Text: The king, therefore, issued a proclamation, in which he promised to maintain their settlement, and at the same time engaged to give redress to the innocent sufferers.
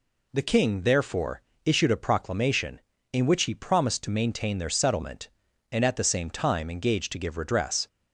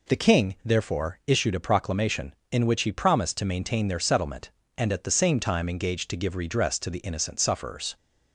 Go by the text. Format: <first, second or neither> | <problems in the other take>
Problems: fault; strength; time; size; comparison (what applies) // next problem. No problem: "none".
second | stops before "to the innocent sufferers"; at 7.8 s